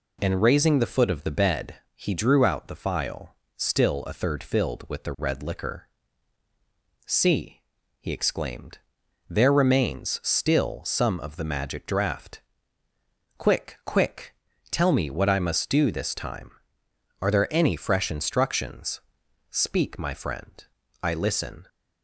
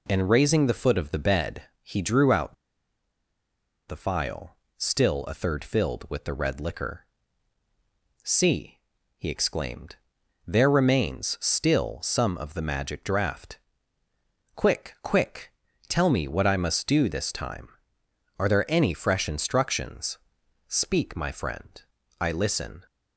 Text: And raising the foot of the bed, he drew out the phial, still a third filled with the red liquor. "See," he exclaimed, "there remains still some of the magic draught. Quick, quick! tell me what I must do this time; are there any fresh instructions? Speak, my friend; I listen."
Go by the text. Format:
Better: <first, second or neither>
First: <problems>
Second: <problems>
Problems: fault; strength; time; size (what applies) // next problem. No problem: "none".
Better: first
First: none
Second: pauses between "out" and "the"; strong; at 2.5 s; 1.3 s long